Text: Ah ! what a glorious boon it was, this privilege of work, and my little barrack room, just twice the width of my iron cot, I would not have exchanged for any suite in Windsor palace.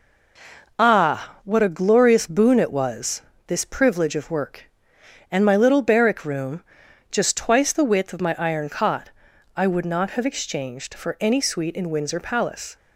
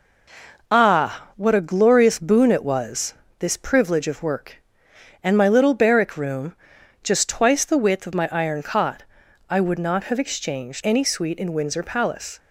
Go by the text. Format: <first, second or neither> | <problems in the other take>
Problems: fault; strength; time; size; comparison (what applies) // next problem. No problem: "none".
first | skips "for"; at 10.8 s